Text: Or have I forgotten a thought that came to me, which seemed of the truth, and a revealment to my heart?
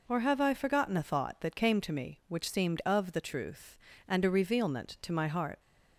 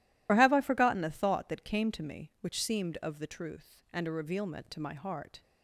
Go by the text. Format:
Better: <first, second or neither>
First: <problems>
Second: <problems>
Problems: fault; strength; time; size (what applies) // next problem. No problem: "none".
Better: first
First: none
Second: loses the start of "Or"; at 0.2 s; 30 ms